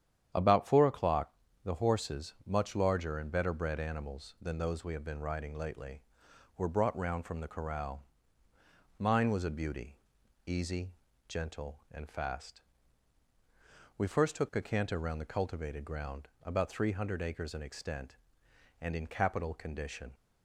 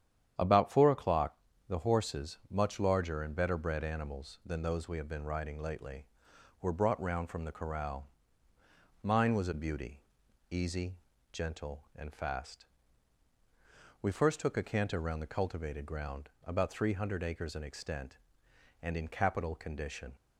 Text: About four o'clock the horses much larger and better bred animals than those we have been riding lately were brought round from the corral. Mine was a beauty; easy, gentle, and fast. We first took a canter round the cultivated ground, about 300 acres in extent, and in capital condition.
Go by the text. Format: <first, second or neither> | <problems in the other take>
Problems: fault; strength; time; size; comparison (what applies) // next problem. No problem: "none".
neither | starts louder than the rest; strong; the same in both // pauses between "o'clock" and "the"; slight; the same in both